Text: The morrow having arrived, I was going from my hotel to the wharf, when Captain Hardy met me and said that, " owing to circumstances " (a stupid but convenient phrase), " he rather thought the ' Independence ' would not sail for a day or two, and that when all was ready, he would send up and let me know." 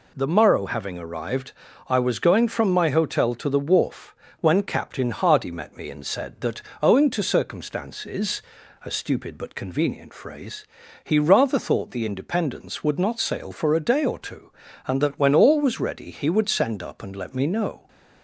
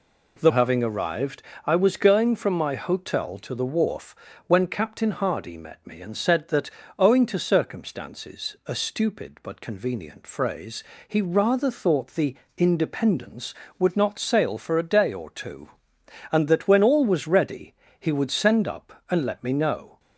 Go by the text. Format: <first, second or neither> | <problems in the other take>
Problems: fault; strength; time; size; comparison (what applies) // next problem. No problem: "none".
first | skips "morrow"; at 0.5 s